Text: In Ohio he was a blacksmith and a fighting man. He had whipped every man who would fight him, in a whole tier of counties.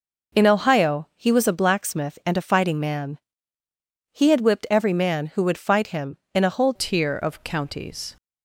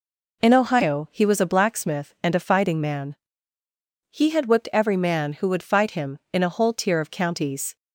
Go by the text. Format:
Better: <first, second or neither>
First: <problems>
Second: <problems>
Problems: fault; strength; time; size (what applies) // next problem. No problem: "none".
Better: second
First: changes voice at "tier"; from 6.7 s on; 1.4 s long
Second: none